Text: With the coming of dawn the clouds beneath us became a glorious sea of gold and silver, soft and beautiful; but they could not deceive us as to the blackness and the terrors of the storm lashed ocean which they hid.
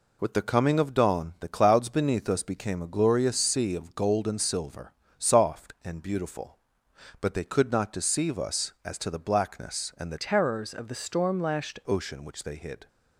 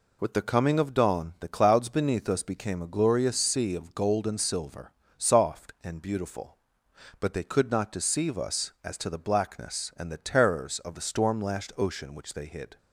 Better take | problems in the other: second | changes voice from "terrors" to "lashed"; from 10.1 to 11.7 s; 1.6 s long

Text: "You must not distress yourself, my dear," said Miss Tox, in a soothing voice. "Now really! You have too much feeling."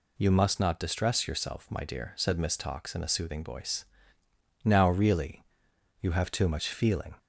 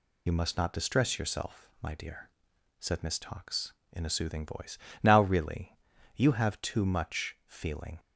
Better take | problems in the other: first | loses the start of "You"; at 0.2 s; 40 ms

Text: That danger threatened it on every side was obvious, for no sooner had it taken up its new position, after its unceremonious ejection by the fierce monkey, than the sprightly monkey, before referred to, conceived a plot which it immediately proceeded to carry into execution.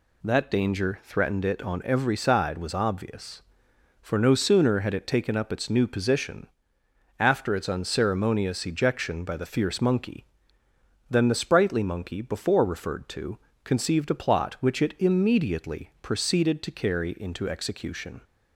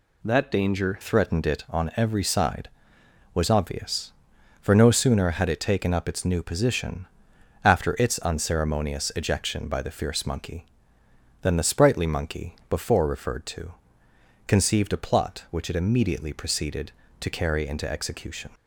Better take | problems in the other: first | changes voice at "threatened"; from 1.0 s on; 17.4 s long

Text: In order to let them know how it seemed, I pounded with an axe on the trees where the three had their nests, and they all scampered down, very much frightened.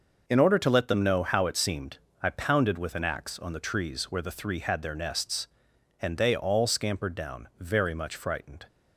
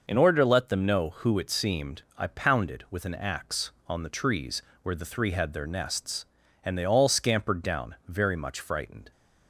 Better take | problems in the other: first | says "who" for "how"; at 1.1 s // pauses between "trees" and "where"; slight; at 4.6 s; 0.20 s long

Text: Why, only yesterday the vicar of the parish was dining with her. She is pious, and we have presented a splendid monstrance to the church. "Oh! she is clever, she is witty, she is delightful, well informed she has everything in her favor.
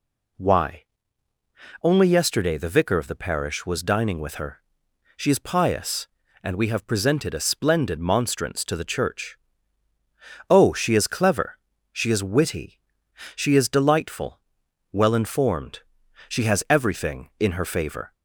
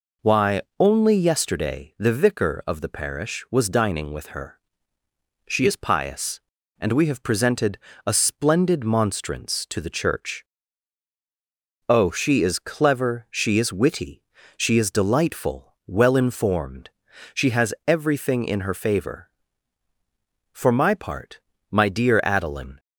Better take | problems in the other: first | pauses between "presented" and "a"; slight; at 7.7 s; 0.28 s long // pauses between "informed" and "she"; at 16.8 s; 0.44 s long; noticeable in the first // goes on to say "For my part my dear Adeline"; strong; from 20.5 s on; 2.2 s long

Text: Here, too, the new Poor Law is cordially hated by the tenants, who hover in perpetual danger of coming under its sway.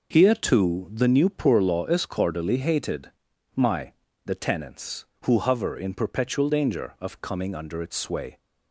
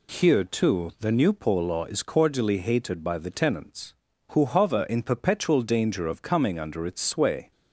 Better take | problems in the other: second | says "my" for "by"; at 3.5 s

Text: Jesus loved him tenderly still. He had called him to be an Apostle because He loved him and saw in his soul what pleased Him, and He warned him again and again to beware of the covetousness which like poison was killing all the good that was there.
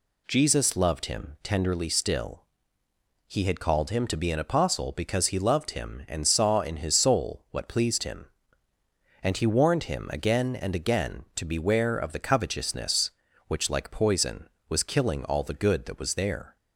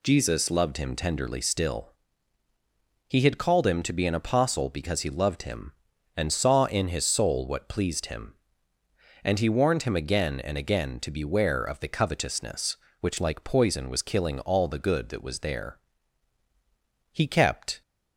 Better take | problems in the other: first | goes on to say "He kept"; noticeable; from 17.1 s on; 0.70 s long

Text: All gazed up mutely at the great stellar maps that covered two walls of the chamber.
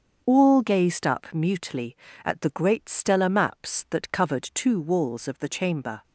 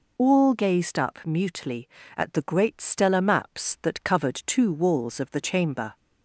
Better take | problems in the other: second | gets quieter; strong; throughout; 8.5 dB

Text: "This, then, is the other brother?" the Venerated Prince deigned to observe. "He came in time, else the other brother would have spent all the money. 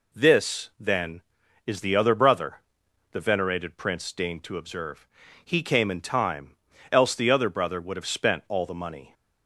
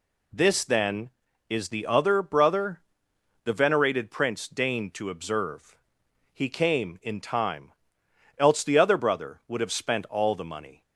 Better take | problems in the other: neither | none

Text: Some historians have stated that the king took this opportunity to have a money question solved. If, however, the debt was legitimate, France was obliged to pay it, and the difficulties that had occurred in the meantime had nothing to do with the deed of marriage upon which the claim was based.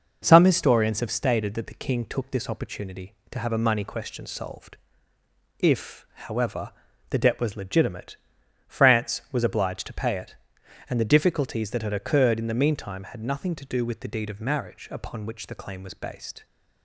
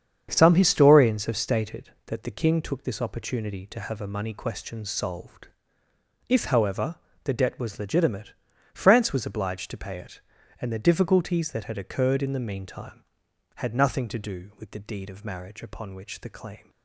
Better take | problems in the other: first | starts louder than the rest; strong; until 1.3 s; 7.5 dB // stops before "was based"; at 16.6 s

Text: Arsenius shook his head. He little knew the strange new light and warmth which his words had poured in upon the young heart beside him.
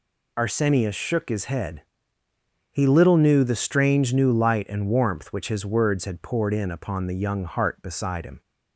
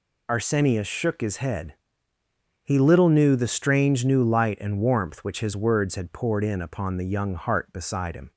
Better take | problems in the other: neither | none

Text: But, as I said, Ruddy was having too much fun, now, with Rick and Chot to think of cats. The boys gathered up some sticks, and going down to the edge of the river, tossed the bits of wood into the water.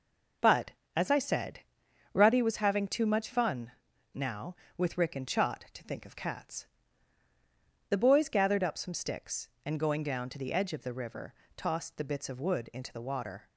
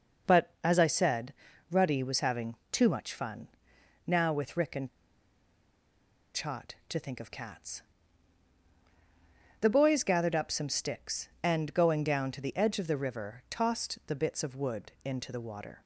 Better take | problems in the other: first | pauses between "having" and "too"; slight; at 2.5 s; 0.16 s long // pauses between "and" and "Chot"; strong; at 4.8 s; 1.4 s long

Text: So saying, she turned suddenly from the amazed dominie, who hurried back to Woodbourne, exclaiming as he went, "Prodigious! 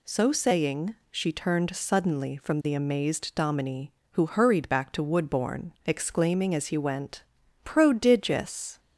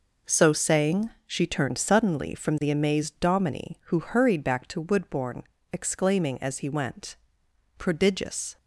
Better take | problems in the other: neither | none

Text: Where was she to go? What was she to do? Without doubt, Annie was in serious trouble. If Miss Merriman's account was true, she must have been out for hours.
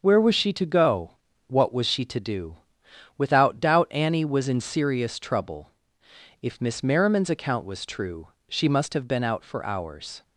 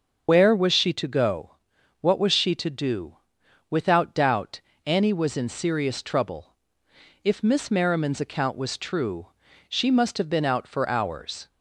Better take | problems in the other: first | loses the start of "Where"; at 0.2 s; 60 ms // starts louder than the rest; until 1.2 s; 6.5 dB; also in the first

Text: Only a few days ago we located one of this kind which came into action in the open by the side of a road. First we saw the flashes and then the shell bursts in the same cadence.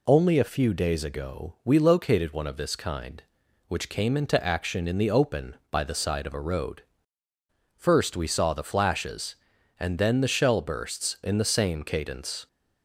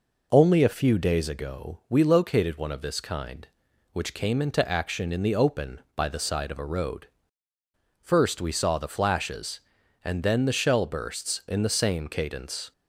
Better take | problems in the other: first | starts louder than the rest; noticeable; until 1.3 s; 4.5 dB

